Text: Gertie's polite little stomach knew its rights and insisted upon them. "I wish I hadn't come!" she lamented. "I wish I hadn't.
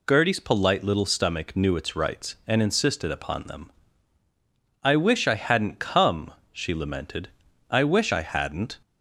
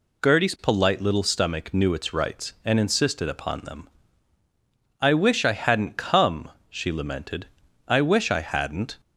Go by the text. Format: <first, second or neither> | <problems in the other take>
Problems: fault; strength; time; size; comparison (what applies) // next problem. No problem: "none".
neither | none